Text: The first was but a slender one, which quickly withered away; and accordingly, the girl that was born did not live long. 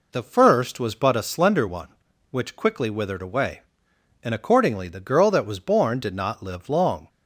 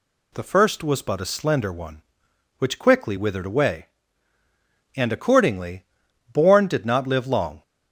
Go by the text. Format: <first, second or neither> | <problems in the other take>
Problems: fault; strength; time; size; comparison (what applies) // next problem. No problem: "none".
first | skips "the girl that was"; at 6.0 s